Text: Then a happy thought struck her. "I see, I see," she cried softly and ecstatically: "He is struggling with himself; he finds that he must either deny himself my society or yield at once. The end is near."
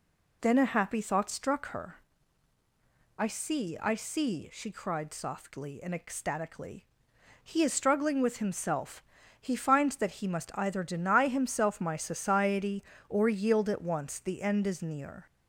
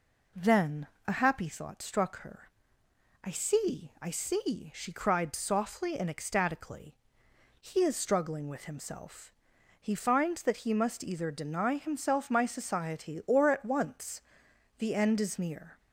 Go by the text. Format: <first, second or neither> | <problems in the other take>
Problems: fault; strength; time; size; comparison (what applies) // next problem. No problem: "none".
first | pauses between "Then" and "a"; slight; at 0.8 s; 0.20 s long // skips "yield"; at 13.4 s